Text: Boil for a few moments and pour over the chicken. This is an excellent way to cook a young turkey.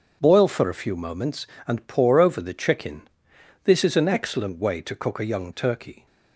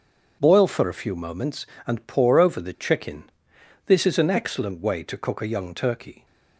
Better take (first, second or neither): neither